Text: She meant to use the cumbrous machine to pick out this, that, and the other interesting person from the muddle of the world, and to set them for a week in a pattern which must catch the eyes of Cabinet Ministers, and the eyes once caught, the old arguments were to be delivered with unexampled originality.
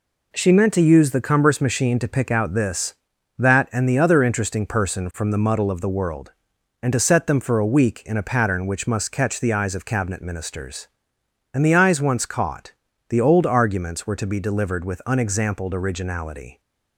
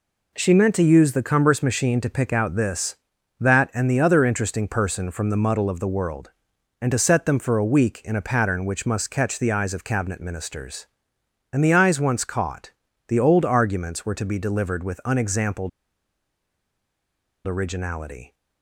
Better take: first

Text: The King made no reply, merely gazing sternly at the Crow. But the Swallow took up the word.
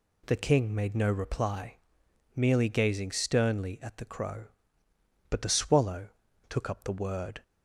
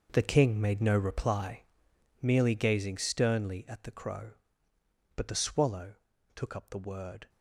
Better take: first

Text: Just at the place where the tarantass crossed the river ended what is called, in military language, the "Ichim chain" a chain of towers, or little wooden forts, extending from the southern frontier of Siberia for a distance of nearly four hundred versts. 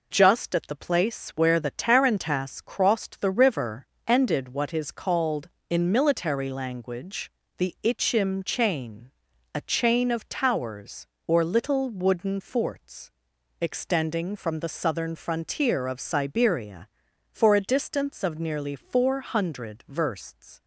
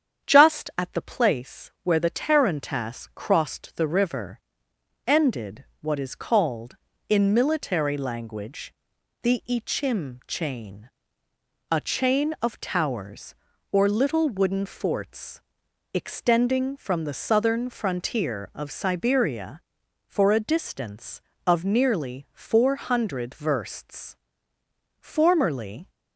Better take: first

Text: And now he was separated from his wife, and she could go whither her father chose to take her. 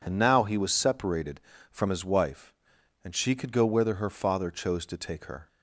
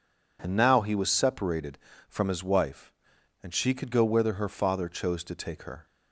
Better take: neither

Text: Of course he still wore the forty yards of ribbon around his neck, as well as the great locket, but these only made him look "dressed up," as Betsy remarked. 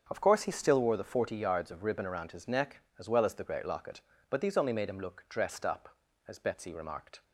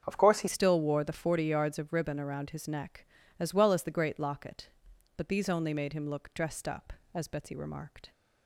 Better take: first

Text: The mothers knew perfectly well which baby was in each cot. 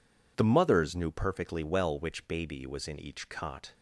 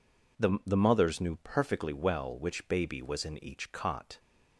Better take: first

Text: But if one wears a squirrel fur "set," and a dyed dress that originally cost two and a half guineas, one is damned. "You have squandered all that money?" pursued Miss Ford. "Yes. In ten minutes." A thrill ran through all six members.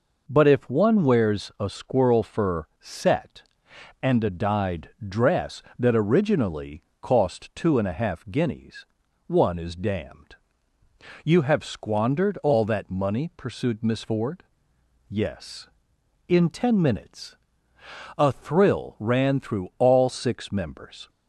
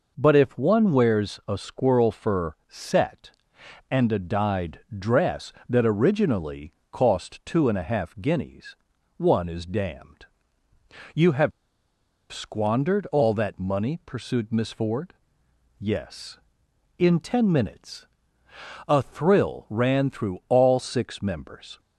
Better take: first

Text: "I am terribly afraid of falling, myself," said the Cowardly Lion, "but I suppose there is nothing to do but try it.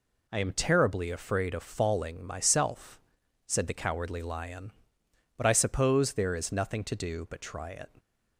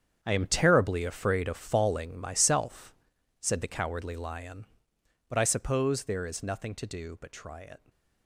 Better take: first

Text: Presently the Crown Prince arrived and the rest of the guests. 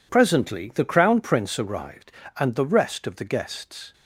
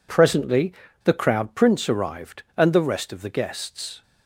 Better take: first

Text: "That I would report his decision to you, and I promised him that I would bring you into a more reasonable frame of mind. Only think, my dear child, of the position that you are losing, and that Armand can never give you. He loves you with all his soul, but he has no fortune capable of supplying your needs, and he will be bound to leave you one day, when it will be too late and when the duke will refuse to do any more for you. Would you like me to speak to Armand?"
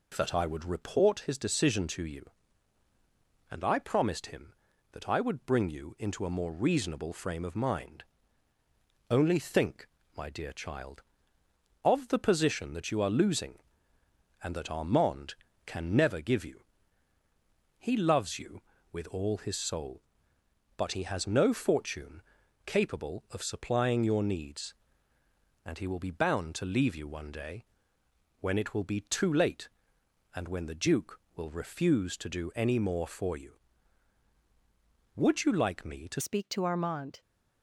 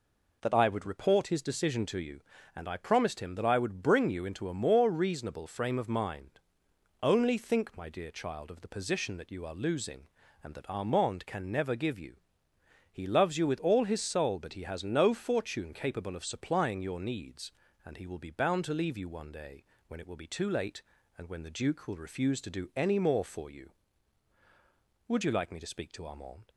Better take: second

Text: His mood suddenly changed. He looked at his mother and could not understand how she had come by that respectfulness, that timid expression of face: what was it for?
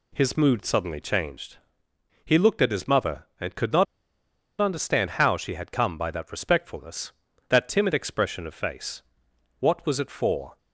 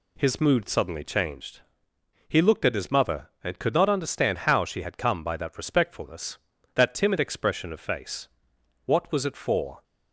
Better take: second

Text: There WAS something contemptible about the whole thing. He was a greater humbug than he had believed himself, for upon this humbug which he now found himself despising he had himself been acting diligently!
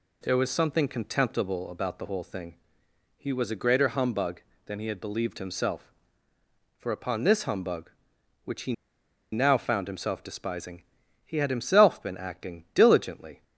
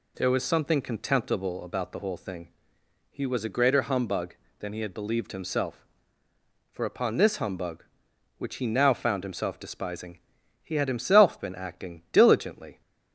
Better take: second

